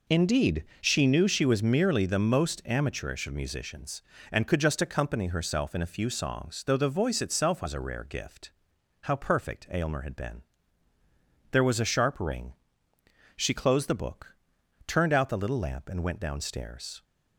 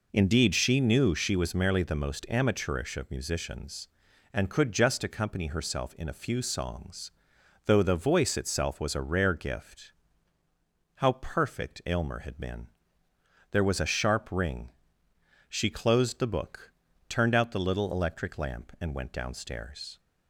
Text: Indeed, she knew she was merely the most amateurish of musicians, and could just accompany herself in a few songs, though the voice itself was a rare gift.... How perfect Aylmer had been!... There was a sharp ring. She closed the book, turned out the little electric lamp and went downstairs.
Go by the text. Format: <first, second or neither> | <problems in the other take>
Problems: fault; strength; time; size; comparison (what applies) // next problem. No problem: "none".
second | skips "electric"; at 15.6 s